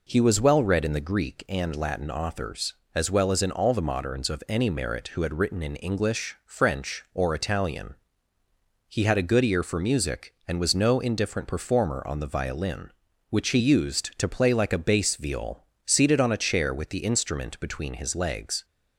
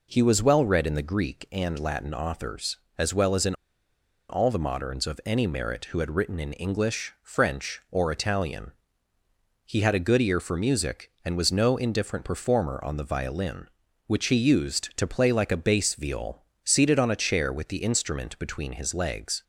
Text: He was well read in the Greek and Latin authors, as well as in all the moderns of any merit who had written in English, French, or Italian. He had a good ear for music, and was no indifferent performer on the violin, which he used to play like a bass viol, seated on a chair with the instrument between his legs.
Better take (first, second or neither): first